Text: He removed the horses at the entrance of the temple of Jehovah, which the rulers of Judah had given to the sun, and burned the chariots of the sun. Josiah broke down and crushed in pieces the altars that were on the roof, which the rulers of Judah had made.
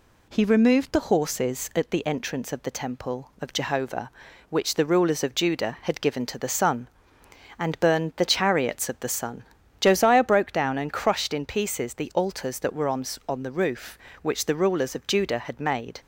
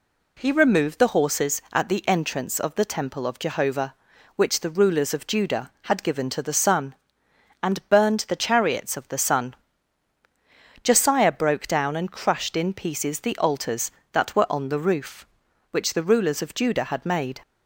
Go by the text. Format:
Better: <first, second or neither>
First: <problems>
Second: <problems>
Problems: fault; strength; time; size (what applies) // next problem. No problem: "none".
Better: second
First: says "on" twice; at 13.2 s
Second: none